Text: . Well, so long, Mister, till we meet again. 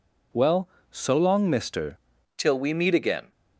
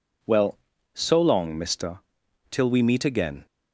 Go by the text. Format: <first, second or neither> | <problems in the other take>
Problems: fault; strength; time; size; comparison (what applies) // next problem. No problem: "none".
second | changes voice at "till"; from 2.3 s on; 1.0 s long